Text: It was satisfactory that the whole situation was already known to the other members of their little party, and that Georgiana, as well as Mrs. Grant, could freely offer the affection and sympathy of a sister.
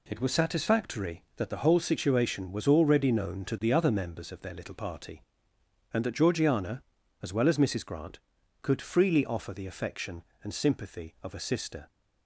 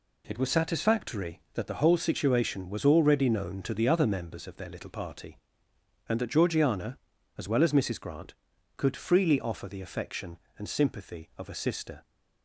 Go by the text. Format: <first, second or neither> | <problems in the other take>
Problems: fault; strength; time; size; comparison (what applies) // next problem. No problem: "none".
neither | none